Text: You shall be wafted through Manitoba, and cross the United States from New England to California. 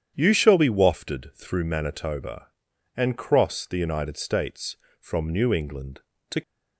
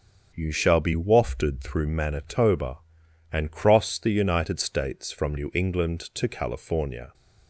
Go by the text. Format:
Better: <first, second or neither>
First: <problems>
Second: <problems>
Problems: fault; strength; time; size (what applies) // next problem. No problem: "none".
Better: second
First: starts louder than the rest; strong; until 1.1 s; 9 dB // stops before "California"; at 6.4 s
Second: starts louder than the rest; until 1.3 s; 7 dB